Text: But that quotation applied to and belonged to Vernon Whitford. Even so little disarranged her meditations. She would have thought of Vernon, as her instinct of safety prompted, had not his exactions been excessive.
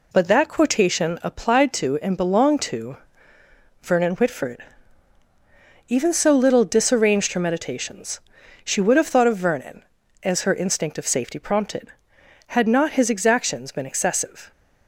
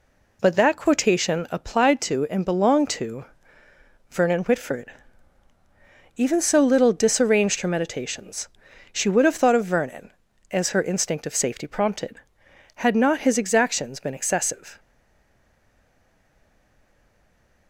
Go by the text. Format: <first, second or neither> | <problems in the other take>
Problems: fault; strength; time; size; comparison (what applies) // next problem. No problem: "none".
first | pauses between "to" and "Vernon"; noticeable; at 3.2 s; 0.84 s long; noticeable in the first // stays silent after the last word; strong; from 14.7 s on; 2.9 s long